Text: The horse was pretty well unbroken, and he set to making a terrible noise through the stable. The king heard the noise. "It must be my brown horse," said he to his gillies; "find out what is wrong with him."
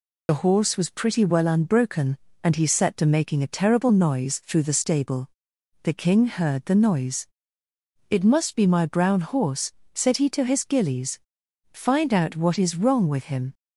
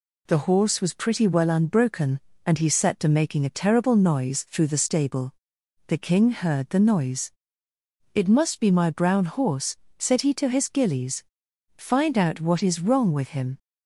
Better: second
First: loses the start of "The"; at 0.2 s; 60 ms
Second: none

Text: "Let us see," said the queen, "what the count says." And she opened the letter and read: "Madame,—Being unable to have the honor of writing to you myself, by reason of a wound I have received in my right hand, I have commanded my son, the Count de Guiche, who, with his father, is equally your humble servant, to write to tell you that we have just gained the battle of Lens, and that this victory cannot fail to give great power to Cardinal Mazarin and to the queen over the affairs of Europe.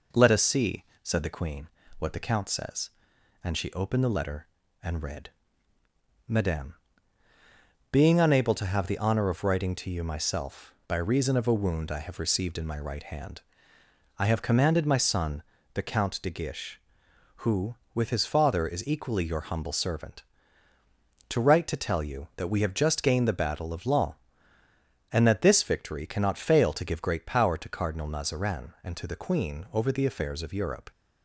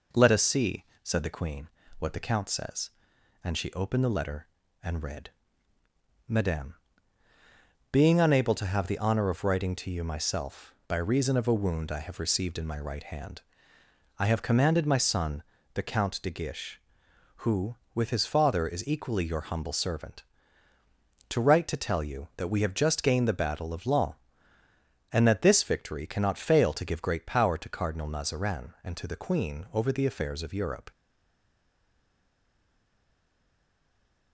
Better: first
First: none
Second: stays silent after the last word; strong; from 30.9 s on; 3.4 s long

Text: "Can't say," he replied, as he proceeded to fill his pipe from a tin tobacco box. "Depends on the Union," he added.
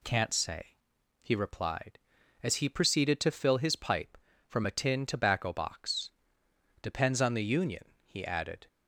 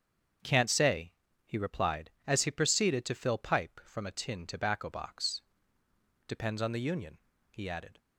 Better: first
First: none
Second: starts louder than the rest; strong; until 1.7 s; 7.5 dB // skips "his"; at 3.3 s

